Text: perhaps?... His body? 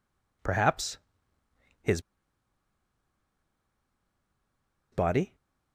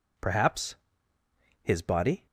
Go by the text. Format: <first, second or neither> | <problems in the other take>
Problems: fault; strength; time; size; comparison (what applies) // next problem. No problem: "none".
second | pauses between "His" and "body"; strong; at 1.9 s; 2.9 s long